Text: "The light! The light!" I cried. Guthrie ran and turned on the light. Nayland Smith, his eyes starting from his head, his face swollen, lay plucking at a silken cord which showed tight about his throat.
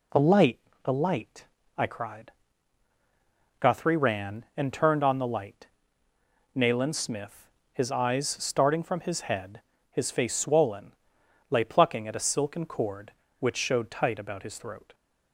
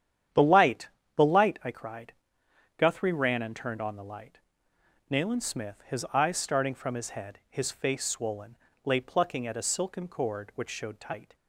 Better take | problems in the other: first | starts louder than the rest; strong; until 1.6 s; 9.5 dB // stops before "about his throat"; at 11.3 s

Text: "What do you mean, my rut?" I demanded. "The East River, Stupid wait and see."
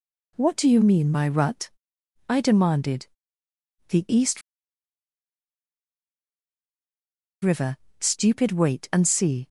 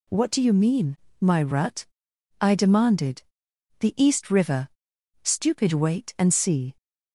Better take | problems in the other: second | pauses between "East" and "River"; strong; at 4.4 s; 3.0 s long

